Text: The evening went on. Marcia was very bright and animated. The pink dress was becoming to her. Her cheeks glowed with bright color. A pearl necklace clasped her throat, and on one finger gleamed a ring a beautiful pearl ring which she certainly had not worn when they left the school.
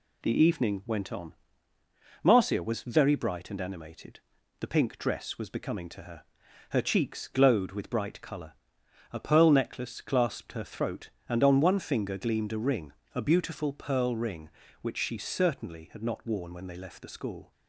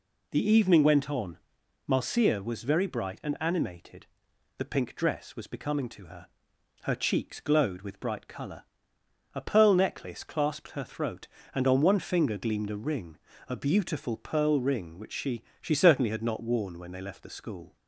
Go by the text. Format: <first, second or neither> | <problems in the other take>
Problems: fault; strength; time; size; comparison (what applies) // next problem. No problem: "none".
first | pauses between "ring" and "a"; slight; at 13.1 s; 0.32 s long; slight in the first // says "she" twice; at 15.6 s